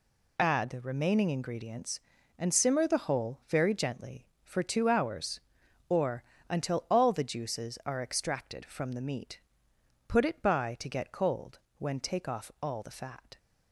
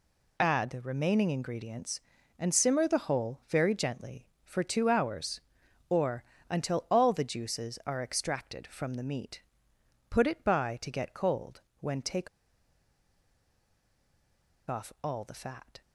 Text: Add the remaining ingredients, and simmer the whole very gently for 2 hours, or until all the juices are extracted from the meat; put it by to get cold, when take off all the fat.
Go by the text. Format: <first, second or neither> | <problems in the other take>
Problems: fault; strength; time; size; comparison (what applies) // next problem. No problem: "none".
first | pauses between "or" and "until"; slight; at 6.2 s; 0.26 s long; slight in the first // pauses between "take" and "off"; strong; at 12.2 s; 2.4 s long